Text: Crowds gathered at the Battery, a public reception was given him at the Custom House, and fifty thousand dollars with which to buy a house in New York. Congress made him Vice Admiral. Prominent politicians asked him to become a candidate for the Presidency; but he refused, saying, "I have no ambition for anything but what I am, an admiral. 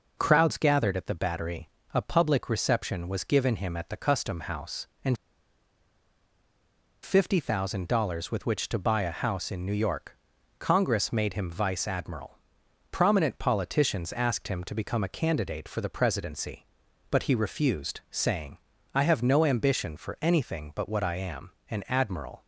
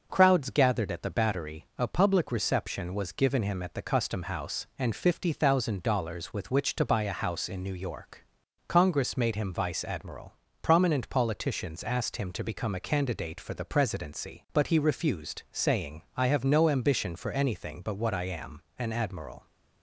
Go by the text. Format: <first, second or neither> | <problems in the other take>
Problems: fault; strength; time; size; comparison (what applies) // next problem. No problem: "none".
second | pauses between "and" and "fifty"; strong; at 5.1 s; 1.8 s long